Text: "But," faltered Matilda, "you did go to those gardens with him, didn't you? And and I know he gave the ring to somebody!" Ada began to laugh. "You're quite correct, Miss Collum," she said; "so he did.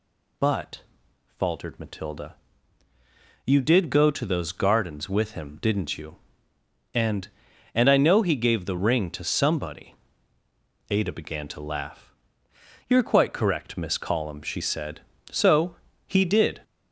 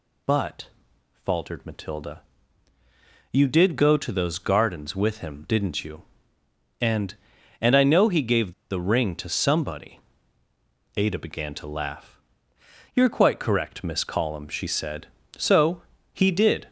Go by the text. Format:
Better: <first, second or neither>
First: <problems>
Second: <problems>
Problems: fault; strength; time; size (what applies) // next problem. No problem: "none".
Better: first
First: pauses between "so" and "he"; slight; at 15.7 s; 0.30 s long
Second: pauses between "gave" and "the"; slight; at 8.5 s; 0.19 s long // pauses between "so" and "he"; slight; at 15.8 s; 0.30 s long